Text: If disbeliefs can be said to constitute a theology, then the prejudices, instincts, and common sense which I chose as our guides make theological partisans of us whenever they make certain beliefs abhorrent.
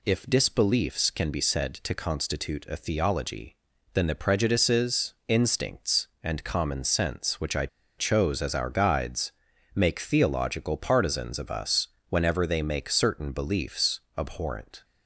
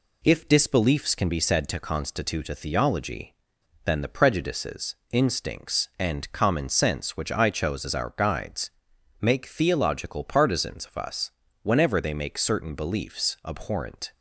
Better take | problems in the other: second | pauses between "I" and "chose"; slight; at 7.6 s; 0.30 s long // pauses between "guides" and "make"; at 9.3 s; 0.42 s long; noticeable in the second // pauses between "us" and "whenever"; slight; at 11.8 s; 0.22 s long; slight in the second

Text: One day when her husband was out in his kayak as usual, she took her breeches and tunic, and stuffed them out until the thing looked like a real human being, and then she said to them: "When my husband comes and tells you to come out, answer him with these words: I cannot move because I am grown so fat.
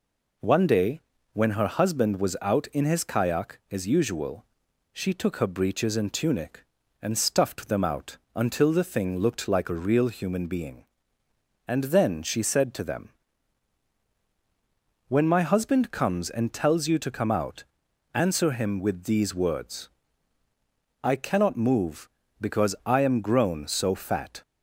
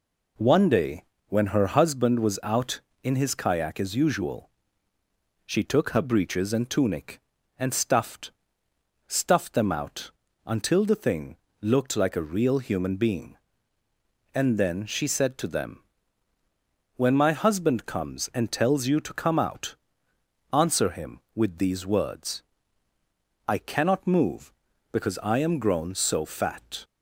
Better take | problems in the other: first | pauses between "day" and "when"; slight; at 1.0 s; 0.26 s long; slight in the first // says "stuffed" twice; at 9.0 s // pauses between "out" and "until"; slight; at 10.0 s; 0.36 s long; slight in the first // pauses between "thing" and "looked"; slight; at 11.3 s; 0.26 s long

